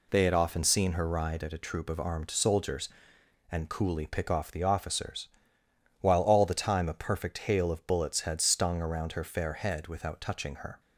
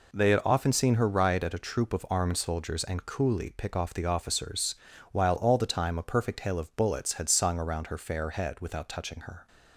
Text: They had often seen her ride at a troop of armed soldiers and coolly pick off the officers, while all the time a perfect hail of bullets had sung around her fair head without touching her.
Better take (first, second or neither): second